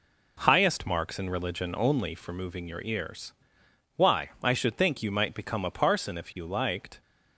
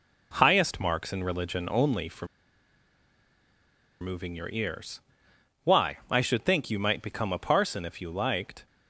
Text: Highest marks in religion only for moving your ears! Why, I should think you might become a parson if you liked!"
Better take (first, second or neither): first